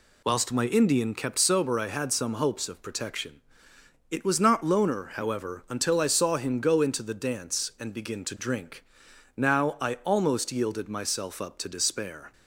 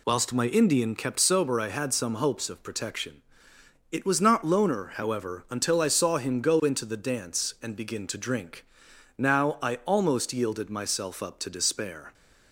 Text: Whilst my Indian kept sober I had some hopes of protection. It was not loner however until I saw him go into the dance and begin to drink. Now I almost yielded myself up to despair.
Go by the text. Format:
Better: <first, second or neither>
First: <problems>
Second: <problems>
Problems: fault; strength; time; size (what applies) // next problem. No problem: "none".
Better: neither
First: none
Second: none